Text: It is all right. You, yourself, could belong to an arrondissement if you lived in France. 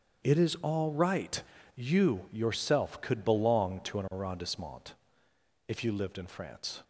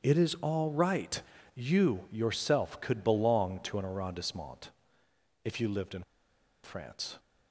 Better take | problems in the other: first | starts louder than the rest; strong; until 1.1 s; 8 dB; strong in the first // pauses between "arrondissement" and "if"; noticeable; at 4.7 s; 0.72 s long; noticeable in the first // pauses between "in" and "France"; noticeable; at 6.0 s; 0.60 s long

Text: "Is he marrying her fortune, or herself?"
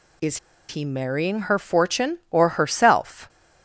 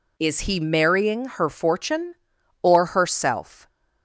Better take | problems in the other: second | pauses between "Is" and "he"; slight; at 0.3 s; 0.30 s long

